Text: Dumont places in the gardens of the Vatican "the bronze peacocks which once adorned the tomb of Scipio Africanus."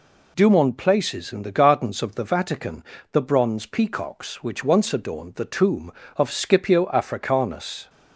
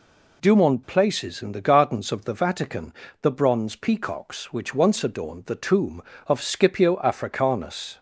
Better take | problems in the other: neither | pauses between "Vatican" and "the"; slight; the same in both

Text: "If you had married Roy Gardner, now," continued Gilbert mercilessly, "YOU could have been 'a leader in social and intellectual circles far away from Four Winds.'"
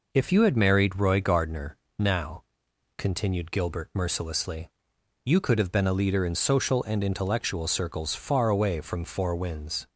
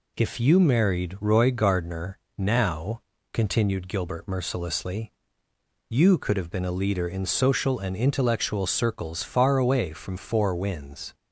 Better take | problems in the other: first | skips "had"; at 0.6 s

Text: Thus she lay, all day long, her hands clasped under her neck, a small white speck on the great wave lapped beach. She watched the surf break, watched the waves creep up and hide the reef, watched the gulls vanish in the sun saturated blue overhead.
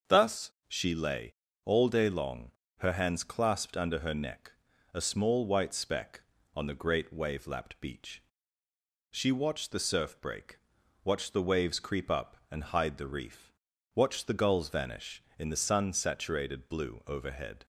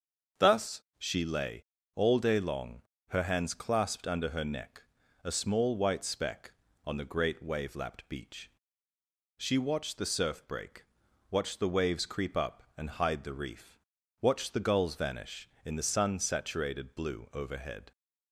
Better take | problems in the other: neither | starts louder than the rest; the same in both // pauses between "Thus" and "she"; slight; the same in both

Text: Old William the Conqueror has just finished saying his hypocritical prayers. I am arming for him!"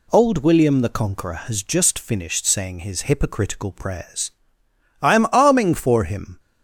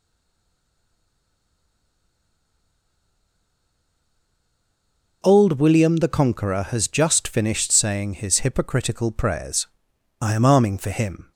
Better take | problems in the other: first | stays silent before the first word; strong; until 5.2 s; 5.2 s long

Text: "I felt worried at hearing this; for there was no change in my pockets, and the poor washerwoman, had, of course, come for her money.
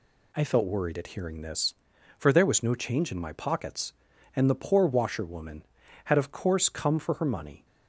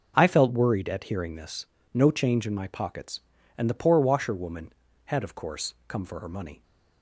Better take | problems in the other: first | skips "for there was"; at 1.7 s

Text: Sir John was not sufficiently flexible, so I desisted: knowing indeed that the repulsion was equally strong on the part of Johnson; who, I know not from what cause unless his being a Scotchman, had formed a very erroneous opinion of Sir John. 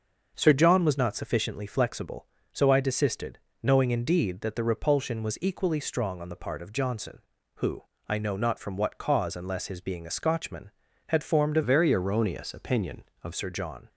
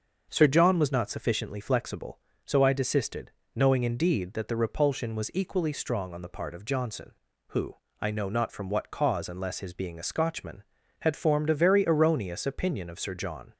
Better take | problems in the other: second | starts louder than the rest; until 1.3 s; 6.5 dB; also in the second // changes voice from "very" to "of"; from 11.6 to 13.3 s; 1.7 s long

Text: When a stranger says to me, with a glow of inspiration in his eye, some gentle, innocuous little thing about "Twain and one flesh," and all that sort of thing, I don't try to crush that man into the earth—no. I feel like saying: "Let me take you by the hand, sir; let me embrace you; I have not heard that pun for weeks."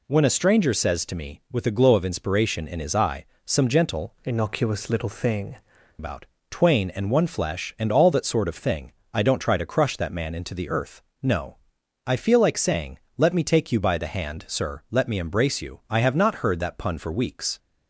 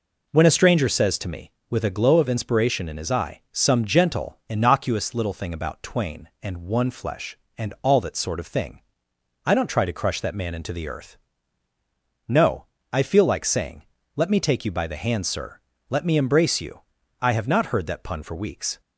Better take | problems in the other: second | changes voice from "innocuous" to "thing"; from 4.2 to 5.5 s; 1.3 s long // pauses between "about" and "Twain"; slight; at 6.2 s; 0.24 s long

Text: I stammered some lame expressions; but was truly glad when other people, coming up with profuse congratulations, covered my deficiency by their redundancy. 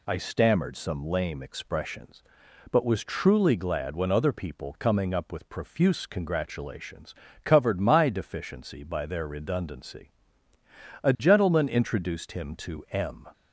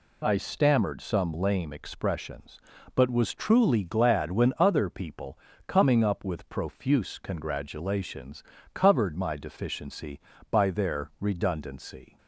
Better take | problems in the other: second | goes on to say "A gentleman introduced him to M"; strong; from 11.0 s on; 2.2 s long

